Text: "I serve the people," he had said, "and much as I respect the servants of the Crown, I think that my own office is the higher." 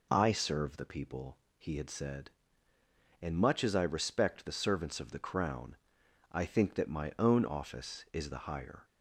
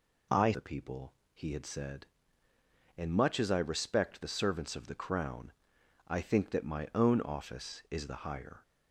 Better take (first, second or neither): first